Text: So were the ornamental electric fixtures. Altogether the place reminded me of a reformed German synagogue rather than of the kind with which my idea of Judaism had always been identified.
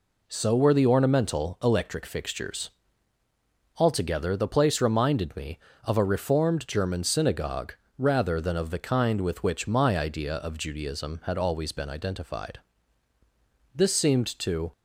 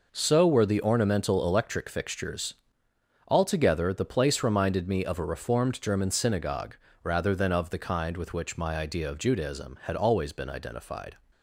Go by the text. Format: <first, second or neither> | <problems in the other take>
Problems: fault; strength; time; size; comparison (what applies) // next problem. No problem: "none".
second | pauses between "synagogue" and "rather"; slight; at 7.7 s; 0.24 s long; slight in the second // goes on to say "This seemed to"; noticeable; from 13.7 s on; 0.98 s long